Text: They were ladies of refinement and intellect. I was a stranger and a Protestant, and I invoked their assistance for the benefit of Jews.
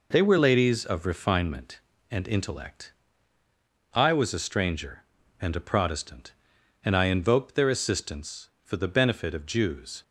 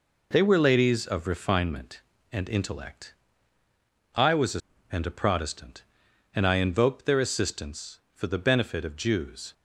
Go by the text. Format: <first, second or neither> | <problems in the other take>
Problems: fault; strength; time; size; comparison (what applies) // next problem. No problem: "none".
first | skips "stranger"; at 4.7 s